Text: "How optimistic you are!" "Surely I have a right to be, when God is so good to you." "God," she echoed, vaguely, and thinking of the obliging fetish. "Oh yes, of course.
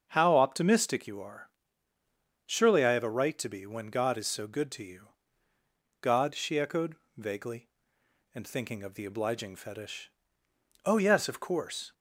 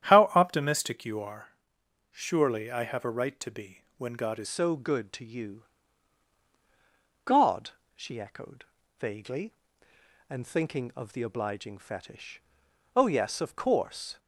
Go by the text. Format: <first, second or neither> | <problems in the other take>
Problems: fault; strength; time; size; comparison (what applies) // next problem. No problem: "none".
first | starts louder than the rest; strong; until 1.1 s; 10 dB; also in the first // changes voice at "so"; from 4.4 s on; 9.7 s long